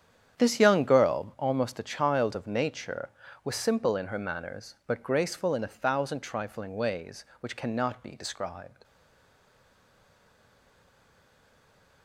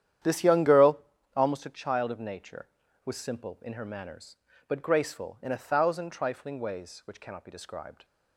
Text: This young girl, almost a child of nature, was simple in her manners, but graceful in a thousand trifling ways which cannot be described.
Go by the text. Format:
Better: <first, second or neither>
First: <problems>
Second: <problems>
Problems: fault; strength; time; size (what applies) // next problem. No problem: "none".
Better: second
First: starts louder than the rest; strong; until 1.4 s; 9 dB // stays silent after the last word; strong; from 8.8 s on; 3.2 s long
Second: starts louder than the rest; strong; until 1.5 s; 10 dB